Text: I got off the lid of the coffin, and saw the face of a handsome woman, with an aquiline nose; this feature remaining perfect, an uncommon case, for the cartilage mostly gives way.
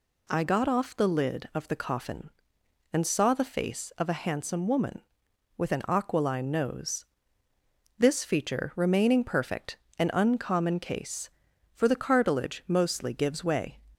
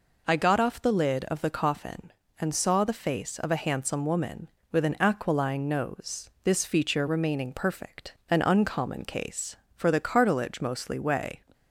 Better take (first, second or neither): first